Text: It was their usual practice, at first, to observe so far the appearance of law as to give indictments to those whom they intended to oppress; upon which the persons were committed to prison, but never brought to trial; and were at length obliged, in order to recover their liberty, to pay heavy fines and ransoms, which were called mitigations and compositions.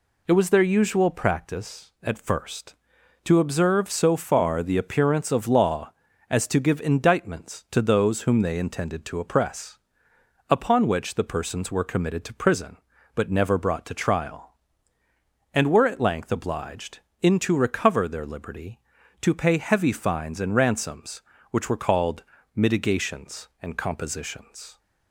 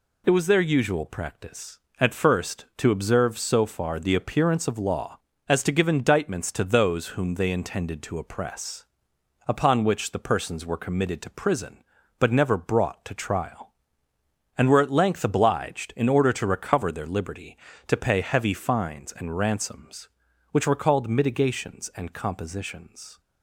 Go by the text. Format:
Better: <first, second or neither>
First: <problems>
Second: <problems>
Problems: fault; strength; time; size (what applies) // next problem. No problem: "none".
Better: second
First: skips "order"; at 17.4 s // pauses between "called" and "mitigations"; slight; at 22.2 s; 0.32 s long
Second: none